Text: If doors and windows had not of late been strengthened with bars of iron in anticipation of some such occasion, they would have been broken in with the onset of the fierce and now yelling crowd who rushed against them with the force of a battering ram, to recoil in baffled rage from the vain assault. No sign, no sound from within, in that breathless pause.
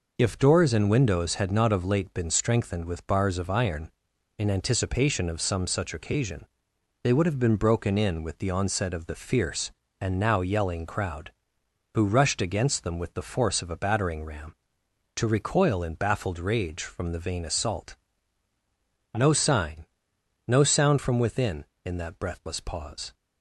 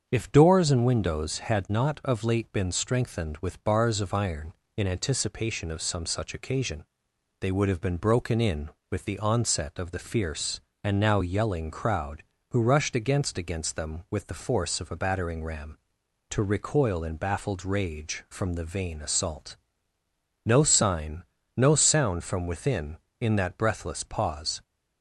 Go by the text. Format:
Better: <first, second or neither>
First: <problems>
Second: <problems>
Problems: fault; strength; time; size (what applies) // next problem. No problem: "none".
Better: first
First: none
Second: starts louder than the rest; strong; until 1.1 s; 7 dB // says "against" twice; at 13.3 s